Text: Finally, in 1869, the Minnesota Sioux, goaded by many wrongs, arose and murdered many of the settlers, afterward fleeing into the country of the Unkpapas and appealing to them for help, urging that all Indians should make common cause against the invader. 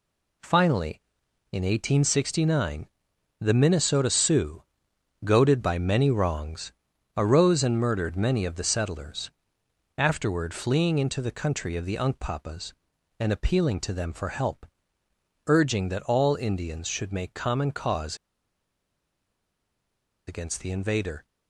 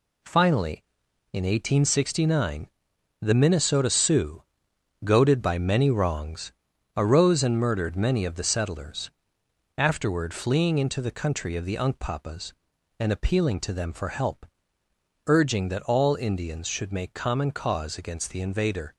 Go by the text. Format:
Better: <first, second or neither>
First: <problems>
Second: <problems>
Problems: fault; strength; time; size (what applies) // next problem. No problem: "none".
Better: second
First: pauses between "cause" and "against"; strong; at 18.1 s; 2.1 s long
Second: none